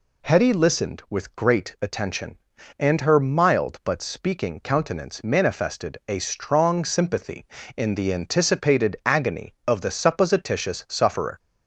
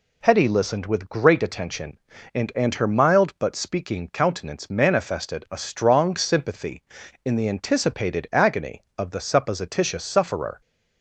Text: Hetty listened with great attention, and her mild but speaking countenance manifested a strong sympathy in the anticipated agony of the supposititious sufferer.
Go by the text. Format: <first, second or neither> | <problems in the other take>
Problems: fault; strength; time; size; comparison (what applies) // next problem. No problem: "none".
first | says "and" twice; at 2.5 s